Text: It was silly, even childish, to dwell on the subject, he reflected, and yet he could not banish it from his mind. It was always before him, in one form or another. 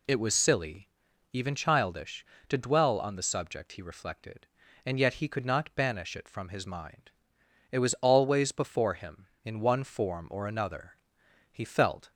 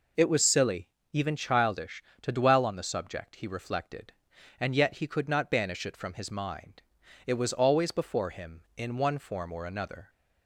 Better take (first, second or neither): second